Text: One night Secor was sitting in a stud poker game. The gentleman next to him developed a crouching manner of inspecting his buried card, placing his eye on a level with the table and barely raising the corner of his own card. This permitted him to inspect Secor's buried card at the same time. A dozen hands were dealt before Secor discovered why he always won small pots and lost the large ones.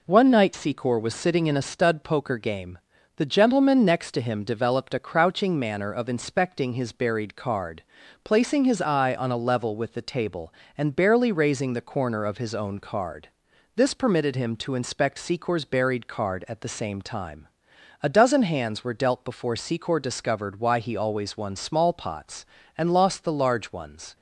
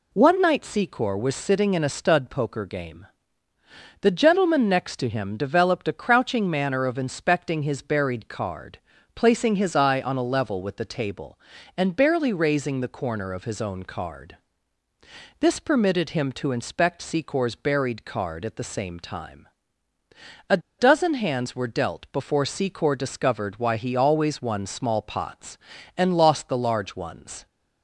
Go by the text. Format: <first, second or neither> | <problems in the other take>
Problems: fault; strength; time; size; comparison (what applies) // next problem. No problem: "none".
first | pauses between "A" and "dozen"; slight; at 20.5 s; 0.20 s long